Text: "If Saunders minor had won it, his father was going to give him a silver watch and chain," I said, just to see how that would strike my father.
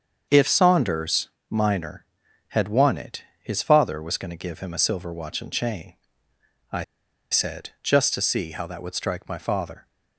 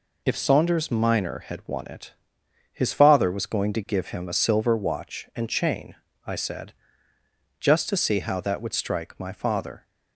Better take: second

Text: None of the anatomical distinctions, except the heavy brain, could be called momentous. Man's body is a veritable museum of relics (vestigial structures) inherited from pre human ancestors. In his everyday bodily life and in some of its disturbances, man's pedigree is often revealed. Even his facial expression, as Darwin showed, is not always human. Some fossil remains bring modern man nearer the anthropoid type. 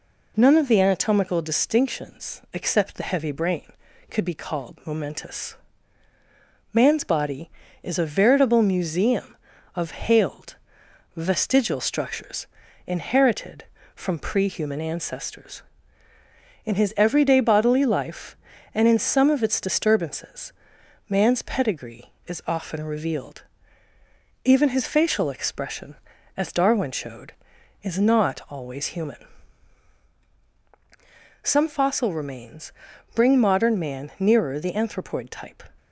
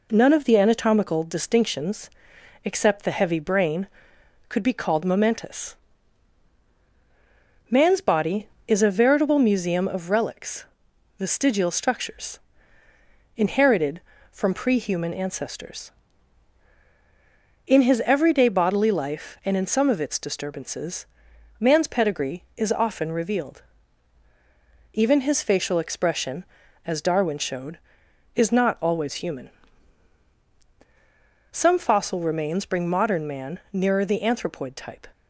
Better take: second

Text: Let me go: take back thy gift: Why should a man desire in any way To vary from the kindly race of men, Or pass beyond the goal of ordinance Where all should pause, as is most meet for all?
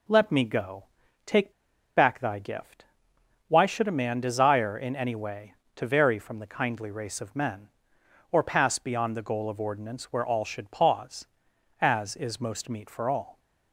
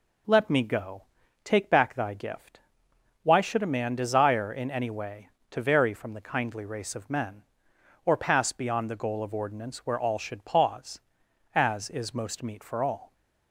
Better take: second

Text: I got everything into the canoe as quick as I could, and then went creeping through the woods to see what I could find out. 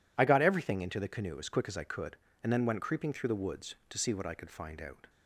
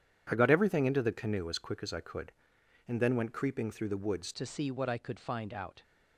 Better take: first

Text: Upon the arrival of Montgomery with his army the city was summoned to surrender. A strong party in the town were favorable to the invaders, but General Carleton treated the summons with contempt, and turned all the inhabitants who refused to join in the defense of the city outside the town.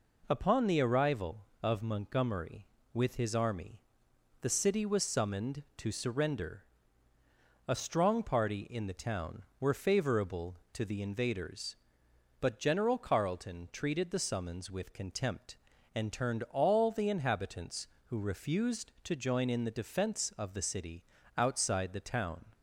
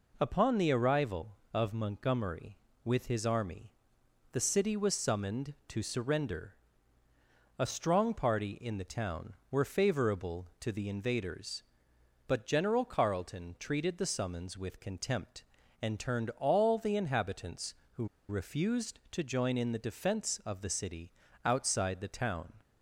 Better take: first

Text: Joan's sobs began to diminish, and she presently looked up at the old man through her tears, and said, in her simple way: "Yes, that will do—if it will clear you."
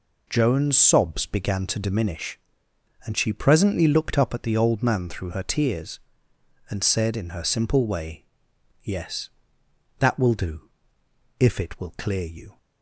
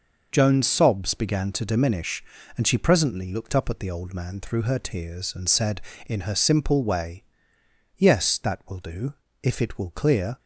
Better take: first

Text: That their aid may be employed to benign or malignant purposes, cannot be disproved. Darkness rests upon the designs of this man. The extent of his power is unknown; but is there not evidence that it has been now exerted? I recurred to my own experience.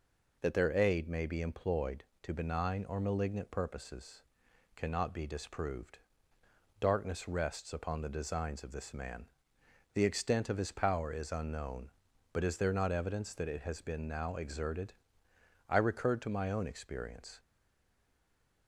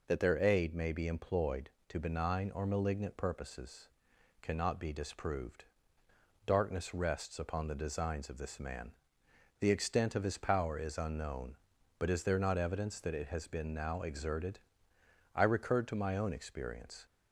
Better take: second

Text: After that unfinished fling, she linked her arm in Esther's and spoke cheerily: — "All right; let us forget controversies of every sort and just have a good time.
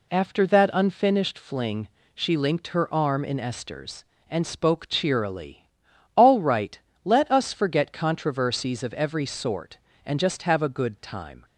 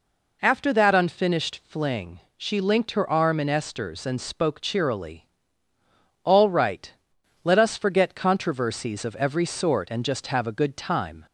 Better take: neither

